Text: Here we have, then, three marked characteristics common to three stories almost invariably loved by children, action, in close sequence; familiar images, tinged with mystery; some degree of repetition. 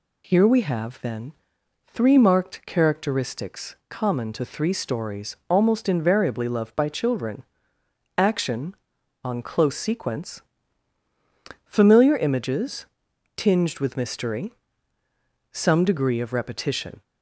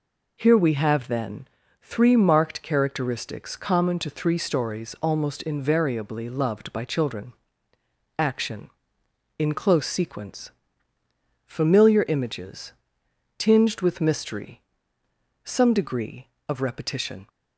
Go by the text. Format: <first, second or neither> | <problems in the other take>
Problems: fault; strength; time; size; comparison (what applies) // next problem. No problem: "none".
second | says "on" for "in"; at 9.2 s